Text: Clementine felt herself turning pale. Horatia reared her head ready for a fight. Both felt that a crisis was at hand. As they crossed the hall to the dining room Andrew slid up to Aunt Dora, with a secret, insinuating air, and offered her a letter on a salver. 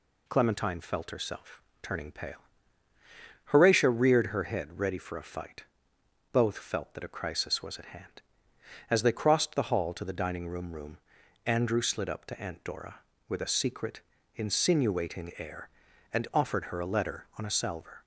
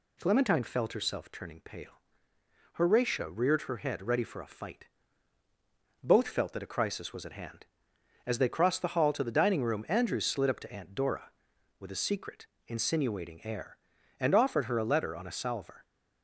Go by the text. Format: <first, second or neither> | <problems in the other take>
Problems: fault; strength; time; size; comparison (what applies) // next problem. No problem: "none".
second | pauses between "herself" and "turning"; slight; at 1.6 s; 0.20 s long // says "room" twice; at 10.7 s